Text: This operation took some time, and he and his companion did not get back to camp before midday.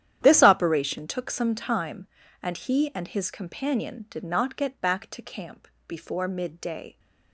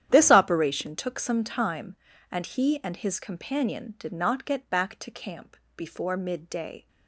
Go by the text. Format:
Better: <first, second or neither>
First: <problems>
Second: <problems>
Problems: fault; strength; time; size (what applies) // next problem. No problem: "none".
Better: neither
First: starts louder than the rest; strong; until 1.2 s; 10.5 dB // pauses between "camp" and "before"; slight; at 5.6 s; 0.18 s long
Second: starts louder than the rest; strong; until 1.1 s; 10.5 dB // pauses between "camp" and "before"; slight; at 5.5 s; 0.18 s long